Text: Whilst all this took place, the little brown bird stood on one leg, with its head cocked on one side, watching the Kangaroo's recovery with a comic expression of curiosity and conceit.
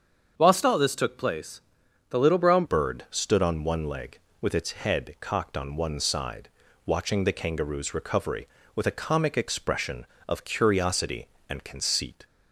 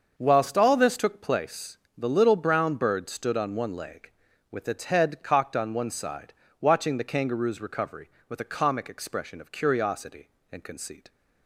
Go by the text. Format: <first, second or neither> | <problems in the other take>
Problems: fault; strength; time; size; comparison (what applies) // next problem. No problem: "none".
second | starts louder than the rest; until 1.3 s; 7 dB; also in the second // changes voice at "bird"; from 2.6 s on; 9.6 s long